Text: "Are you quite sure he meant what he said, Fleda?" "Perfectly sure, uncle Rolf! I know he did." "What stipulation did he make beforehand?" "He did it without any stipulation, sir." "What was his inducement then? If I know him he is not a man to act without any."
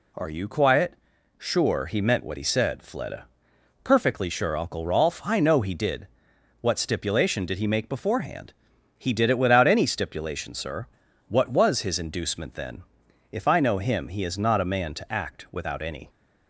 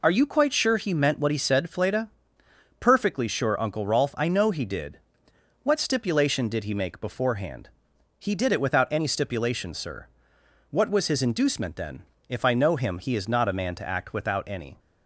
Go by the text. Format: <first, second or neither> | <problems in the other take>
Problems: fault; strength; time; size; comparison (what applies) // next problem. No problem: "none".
second | says "quiet" for "quite"; at 0.4 s